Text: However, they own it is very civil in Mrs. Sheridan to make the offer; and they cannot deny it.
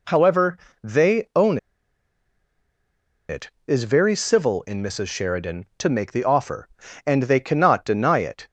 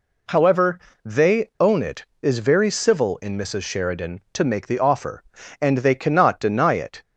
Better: second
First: pauses between "own" and "it"; strong; at 1.5 s; 1.7 s long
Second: none

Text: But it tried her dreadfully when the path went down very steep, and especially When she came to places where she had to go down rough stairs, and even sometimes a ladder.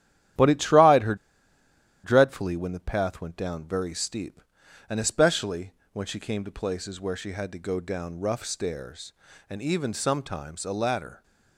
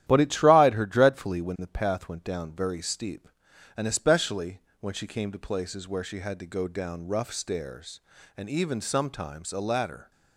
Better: second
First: starts louder than the rest; strong; until 2.2 s; 12 dB // pauses between "her" and "dreadfully"; noticeable; at 1.1 s; 0.88 s long // pauses between "especially" and "When"; slight; at 5.7 s; 0.20 s long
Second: starts louder than the rest; strong; until 1.0 s; 12 dB // pauses between "especially" and "When"; slight; at 4.6 s; 0.20 s long

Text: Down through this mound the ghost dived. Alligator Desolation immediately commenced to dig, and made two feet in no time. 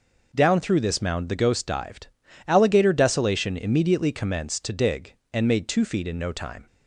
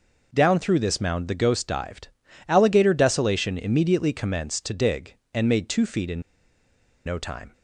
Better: first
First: none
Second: pauses between "in" and "no"; noticeable; at 6.2 s; 0.84 s long

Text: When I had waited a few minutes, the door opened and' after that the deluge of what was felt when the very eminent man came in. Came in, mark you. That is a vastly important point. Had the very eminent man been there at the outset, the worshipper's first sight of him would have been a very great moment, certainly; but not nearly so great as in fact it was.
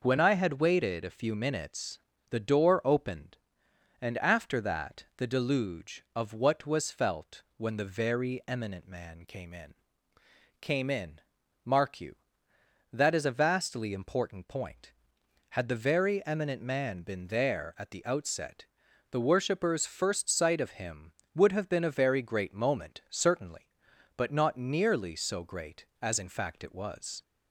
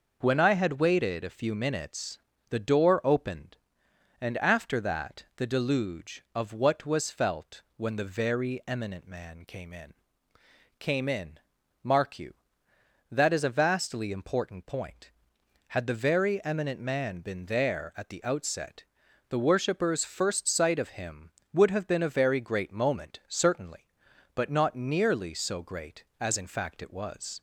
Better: neither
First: none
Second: none

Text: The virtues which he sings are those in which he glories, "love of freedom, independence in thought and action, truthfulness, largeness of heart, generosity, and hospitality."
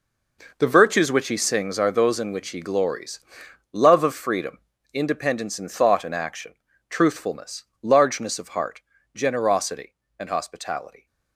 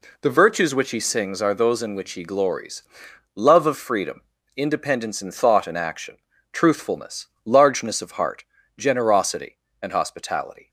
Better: second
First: gets quieter; strong; throughout; 12 dB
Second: none

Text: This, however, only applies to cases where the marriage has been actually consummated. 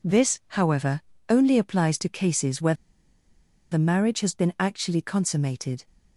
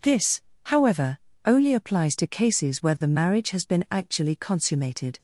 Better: second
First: pauses between "where" and "the"; noticeable; at 2.7 s; 0.97 s long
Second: none

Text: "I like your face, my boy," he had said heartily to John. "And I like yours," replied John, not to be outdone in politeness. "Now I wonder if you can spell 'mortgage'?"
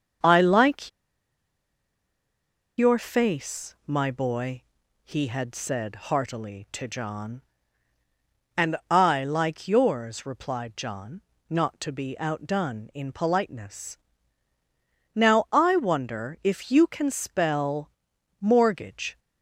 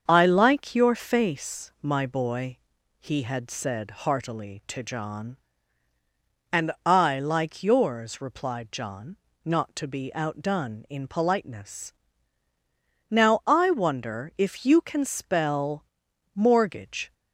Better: second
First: starts louder than the rest; until 3.1 s; 7 dB // pauses between "like" and "your"; strong; at 0.8 s; 1.8 s long // pauses between "spell" and "mortgage"; noticeable; at 17.9 s; 0.50 s long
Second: starts louder than the rest; until 1.0 s; 7 dB // pauses between "spell" and "mortgage"; noticeable; at 15.8 s; 0.50 s long

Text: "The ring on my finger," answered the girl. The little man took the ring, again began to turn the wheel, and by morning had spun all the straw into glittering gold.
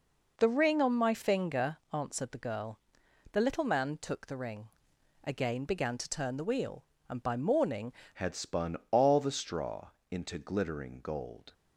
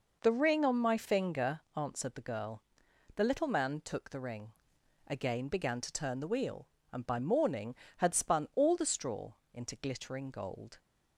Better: second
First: changes voice at "had"; from 8.1 s on; 3.4 s long // pauses between "straw" and "into"; slight; at 9.8 s; 0.22 s long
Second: pauses between "straw" and "into"; slight; at 9.3 s; 0.18 s long

